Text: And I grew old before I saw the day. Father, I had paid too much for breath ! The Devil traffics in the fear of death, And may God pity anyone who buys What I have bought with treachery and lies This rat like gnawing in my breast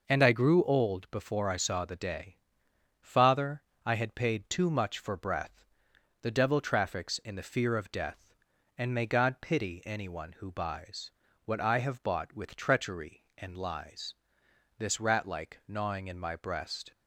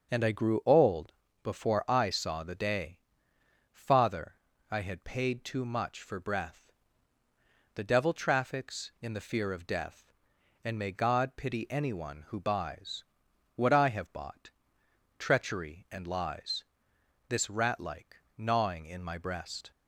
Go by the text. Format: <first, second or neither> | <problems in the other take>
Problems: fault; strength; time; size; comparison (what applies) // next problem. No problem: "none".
first | pauses between "old" and "before"; slight; at 1.1 s; 0.30 s long // pauses between "buys" and "What"; noticeable; at 13.0 s; 0.50 s long; slight in the first // skips "with"; at 14.8 s // pauses between "lies" and "This"; noticeable; at 16.6 s; 0.64 s long; noticeable in the first // pauses between "like" and "gnawing"; slight; at 18.1 s; 0.20 s long